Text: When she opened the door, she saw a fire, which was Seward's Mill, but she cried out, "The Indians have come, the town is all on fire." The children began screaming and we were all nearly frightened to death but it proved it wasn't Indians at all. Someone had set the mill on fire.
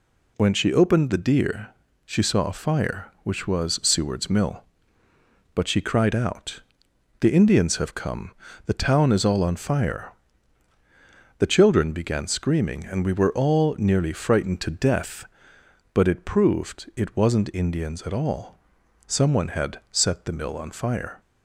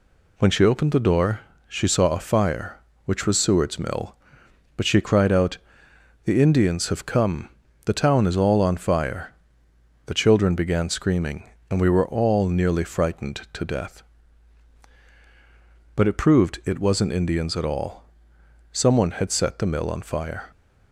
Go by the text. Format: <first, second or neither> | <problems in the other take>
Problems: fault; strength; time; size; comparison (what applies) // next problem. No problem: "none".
second | says "deer" for "door"; at 1.1 s